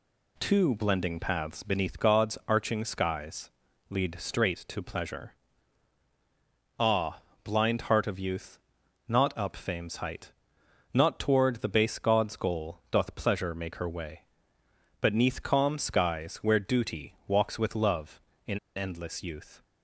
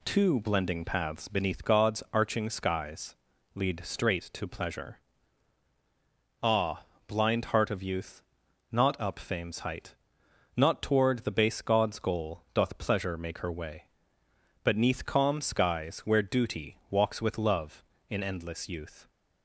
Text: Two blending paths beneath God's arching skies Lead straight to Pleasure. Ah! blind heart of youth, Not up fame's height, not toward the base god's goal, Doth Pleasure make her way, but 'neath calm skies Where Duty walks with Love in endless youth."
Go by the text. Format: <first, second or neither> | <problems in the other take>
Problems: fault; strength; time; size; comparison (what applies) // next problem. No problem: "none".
second | pauses between "skies" and "Lead"; at 3.5 s; 0.38 s long; also in the second // pauses between "in" and "endless"; slight; at 18.5 s; 0.18 s long